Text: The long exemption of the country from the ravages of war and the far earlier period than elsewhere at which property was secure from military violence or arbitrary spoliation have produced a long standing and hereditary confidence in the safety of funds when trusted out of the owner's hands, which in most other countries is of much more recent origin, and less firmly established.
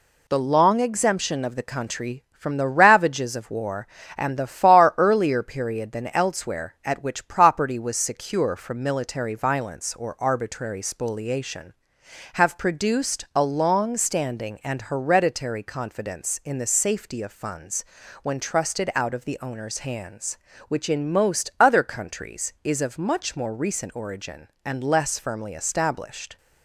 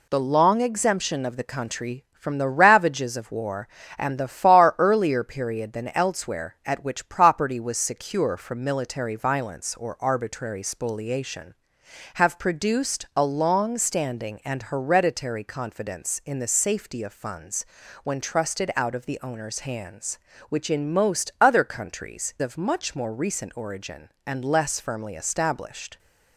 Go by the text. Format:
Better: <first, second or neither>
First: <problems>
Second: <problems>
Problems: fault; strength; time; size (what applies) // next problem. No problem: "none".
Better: first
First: pauses between "funds" and "when"; at 17.8 s; 0.38 s long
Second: pauses between "funds" and "when"; at 17.6 s; 0.38 s long // skips "is"; at 22.3 s